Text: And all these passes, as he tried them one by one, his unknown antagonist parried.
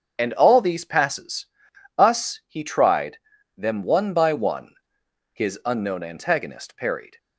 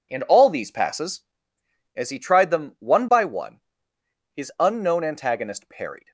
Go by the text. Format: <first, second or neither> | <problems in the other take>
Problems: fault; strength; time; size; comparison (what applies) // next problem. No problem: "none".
second | starts louder than the rest; until 1.1 s; 6.5 dB // says "us" for "as"; at 1.9 s // pauses between "tried" and "them"; at 3.1 s; 0.40 s long